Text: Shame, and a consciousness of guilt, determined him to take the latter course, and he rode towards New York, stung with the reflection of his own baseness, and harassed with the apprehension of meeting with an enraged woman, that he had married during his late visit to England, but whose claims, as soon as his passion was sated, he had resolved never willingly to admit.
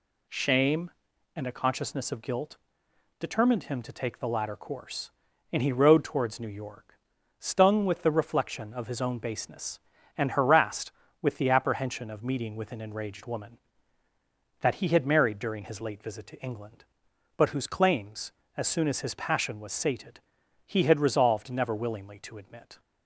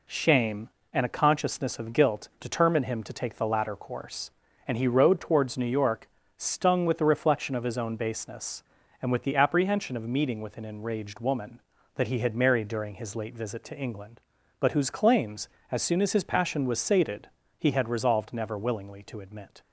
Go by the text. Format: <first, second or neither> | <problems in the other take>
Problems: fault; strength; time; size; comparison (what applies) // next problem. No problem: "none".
first | skips "harassed"; at 9.1 s